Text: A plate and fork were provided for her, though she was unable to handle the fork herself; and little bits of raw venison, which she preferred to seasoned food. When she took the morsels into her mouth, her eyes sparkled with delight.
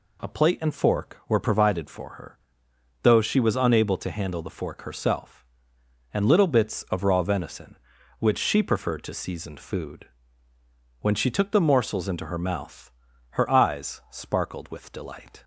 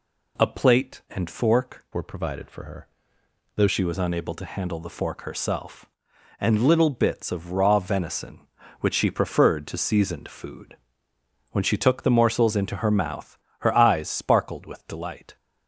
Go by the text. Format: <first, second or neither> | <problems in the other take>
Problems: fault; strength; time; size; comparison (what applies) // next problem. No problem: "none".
first | changes voice from "were" to "though"; from 1.9 to 3.6 s; 1.7 s long